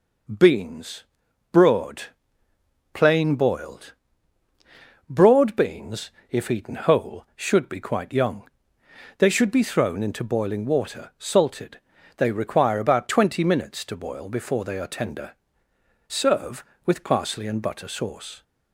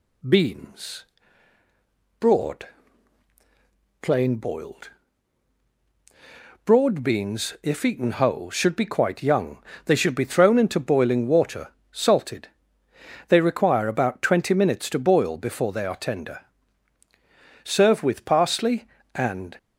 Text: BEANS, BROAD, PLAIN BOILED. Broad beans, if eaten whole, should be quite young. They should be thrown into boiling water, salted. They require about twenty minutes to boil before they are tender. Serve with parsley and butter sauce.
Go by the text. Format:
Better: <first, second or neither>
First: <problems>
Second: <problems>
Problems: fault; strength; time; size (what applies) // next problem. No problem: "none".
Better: first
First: none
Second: stops before "butter sauce"; at 19.5 s